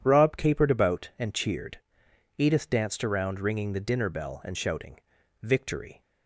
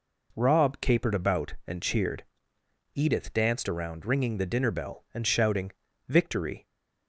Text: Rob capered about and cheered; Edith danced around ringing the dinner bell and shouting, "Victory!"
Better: neither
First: none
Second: none

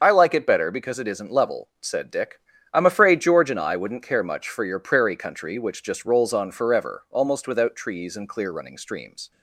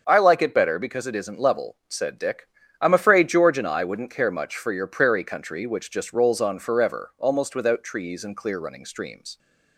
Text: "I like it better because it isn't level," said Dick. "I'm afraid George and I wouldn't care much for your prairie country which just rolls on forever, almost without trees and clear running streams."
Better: second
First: loses the start of "I"; at 0.0 s; 30 ms // starts louder than the rest; until 1.0 s; 6.5 dB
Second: starts louder than the rest; until 1.0 s; 7 dB

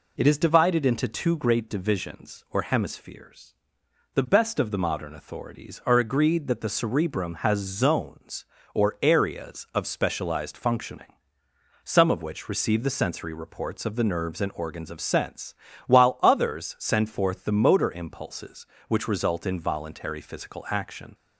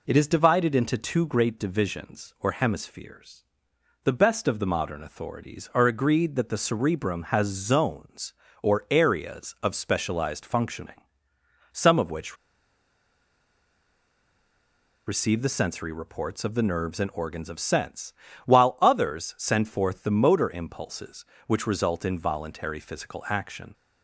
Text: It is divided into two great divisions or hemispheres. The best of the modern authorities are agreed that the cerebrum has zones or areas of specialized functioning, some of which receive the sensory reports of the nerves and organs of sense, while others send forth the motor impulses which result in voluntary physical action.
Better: first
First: none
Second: pauses between "which" and "receive"; strong; at 12.3 s; 2.7 s long

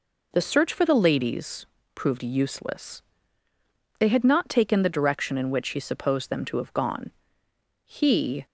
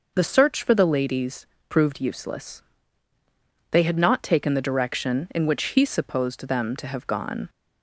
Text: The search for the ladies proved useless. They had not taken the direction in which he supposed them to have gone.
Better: second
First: pauses between "ladies" and "proved"; slight; at 1.6 s; 0.28 s long // goes on to say "He"; from 7.8 s on; 0.60 s long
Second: pauses between "ladies" and "proved"; slight; at 1.4 s; 0.24 s long

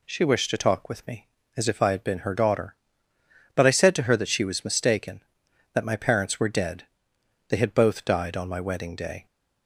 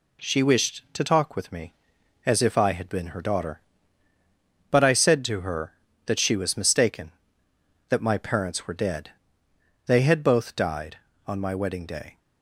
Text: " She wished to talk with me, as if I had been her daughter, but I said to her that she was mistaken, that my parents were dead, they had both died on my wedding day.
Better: neither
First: none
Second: none

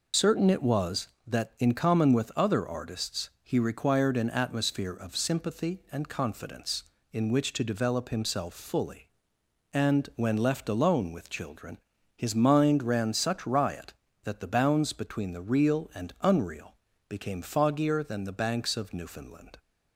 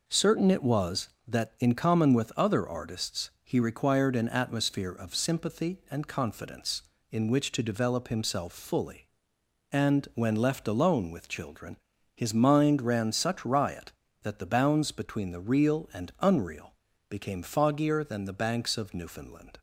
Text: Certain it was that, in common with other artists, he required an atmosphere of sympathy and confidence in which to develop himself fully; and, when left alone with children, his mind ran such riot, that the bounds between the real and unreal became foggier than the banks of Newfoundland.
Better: second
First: loses the start of "Certain"; at 0.1 s; 65 ms // pauses between "unreal" and "became"; slight; at 16.7 s; 0.32 s long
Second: pauses between "unreal" and "became"; slight; at 16.7 s; 0.34 s long

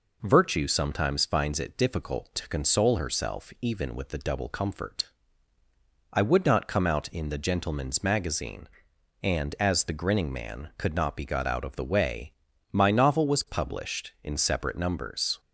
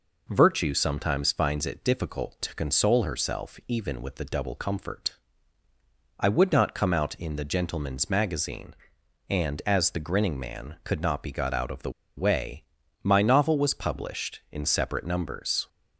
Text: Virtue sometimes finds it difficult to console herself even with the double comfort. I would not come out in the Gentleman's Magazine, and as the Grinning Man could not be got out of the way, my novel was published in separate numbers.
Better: first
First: none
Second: pauses between "the" and "way"; slight; at 11.8 s; 0.27 s long

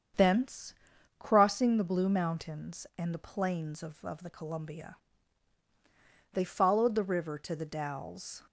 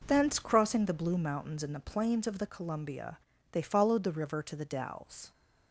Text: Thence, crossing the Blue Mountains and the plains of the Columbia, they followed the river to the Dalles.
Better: second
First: starts louder than the rest; strong; until 1.6 s; 7.5 dB // says "of" twice; at 4.0 s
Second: none

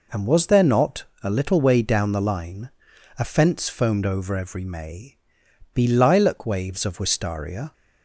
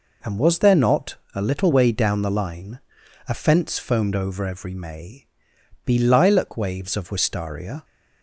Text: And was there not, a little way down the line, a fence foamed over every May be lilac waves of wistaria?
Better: neither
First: pauses between "May" and "be"; noticeable; at 5.1 s; 0.56 s long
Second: pauses between "May" and "be"; noticeable; at 5.2 s; 0.58 s long

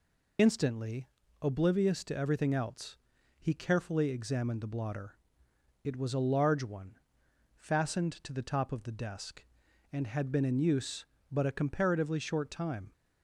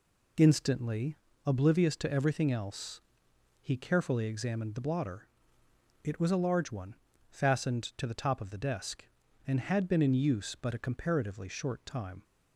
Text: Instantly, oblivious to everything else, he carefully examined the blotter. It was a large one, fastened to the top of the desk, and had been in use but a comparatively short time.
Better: second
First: loses the start of "Instantly"; at 0.3 s; 55 ms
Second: none

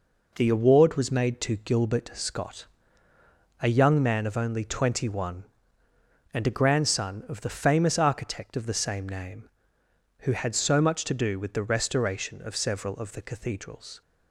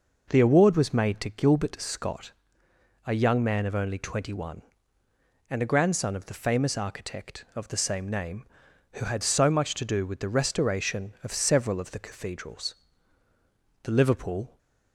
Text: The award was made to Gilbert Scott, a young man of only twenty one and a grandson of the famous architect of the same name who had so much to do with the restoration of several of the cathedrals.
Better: first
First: none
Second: goes on to say "The Liverpool"; noticeable; from 13.8 s on; 0.74 s long

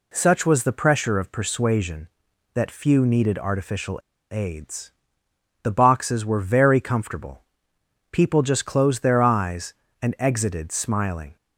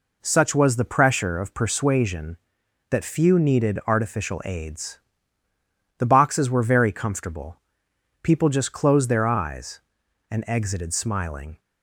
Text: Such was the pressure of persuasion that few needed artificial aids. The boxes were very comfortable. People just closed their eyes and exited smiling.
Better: second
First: pauses between "artificial" and "aids"; slight; at 3.9 s; 0.33 s long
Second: none

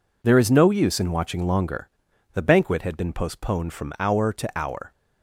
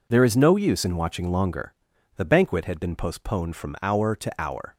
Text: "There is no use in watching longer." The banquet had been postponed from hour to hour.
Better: neither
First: none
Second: none

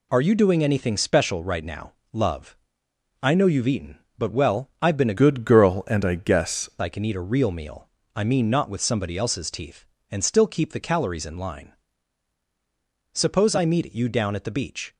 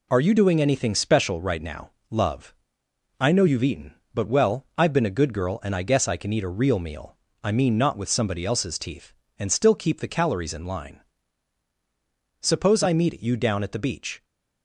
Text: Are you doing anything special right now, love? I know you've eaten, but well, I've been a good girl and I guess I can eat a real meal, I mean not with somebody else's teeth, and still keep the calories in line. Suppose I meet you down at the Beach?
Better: second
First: changes voice from "good" to "guess"; from 5.1 to 6.6 s; 1.5 s long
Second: none

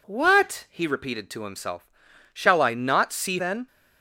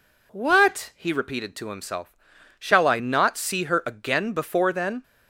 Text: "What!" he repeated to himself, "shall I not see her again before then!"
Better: second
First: skips "her again before"; at 3.3 s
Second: none

